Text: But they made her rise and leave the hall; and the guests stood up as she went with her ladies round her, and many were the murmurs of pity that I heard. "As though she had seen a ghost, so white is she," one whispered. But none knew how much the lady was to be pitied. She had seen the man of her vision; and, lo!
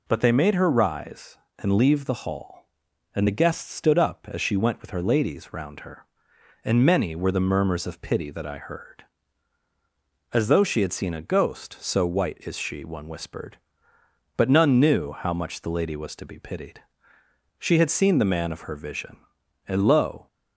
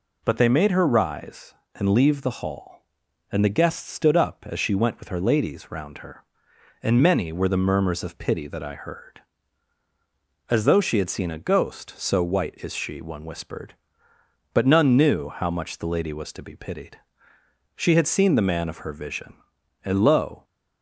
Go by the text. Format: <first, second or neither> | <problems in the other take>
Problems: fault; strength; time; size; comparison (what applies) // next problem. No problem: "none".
neither | none